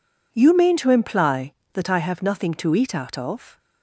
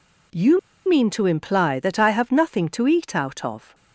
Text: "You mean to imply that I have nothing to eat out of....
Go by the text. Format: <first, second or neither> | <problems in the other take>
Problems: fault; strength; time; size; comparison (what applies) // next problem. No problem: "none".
first | pauses between "You" and "mean"; slight; at 0.5 s; 0.29 s long